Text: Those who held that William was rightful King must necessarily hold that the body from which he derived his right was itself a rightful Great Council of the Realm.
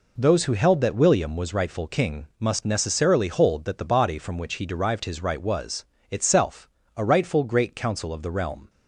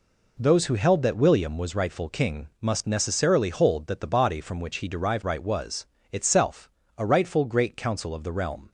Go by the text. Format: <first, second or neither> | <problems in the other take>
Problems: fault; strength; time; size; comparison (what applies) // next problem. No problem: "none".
first | skips "his"; at 5.2 s // pauses between "was" and "itself"; slight; at 5.8 s; 0.26 s long; slight in the first // pauses between "itself" and "a"; slight; at 6.7 s; 0.26 s long; slight in the first